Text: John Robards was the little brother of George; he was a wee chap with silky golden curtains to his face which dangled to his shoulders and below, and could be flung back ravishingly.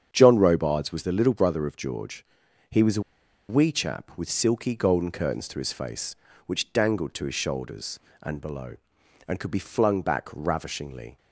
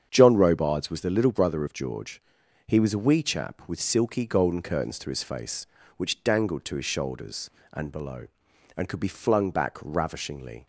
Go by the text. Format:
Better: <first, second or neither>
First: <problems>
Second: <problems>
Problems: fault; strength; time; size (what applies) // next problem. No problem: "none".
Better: second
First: starts louder than the rest; strong; until 1.1 s; 8 dB // pauses between "a" and "wee"; noticeable; at 3.0 s; 0.47 s long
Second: starts louder than the rest; strong; until 1.1 s; 8 dB